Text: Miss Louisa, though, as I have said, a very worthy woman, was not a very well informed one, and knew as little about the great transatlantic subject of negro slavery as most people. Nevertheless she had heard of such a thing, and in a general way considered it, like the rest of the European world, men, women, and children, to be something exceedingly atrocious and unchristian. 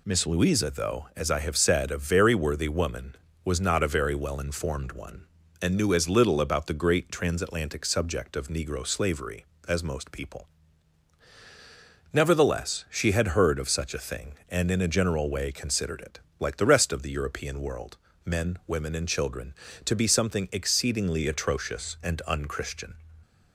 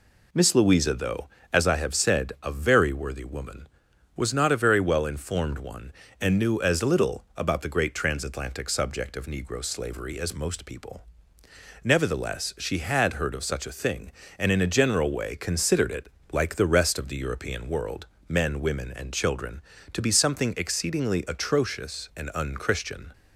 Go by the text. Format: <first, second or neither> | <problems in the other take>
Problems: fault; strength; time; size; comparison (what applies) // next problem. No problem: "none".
neither | none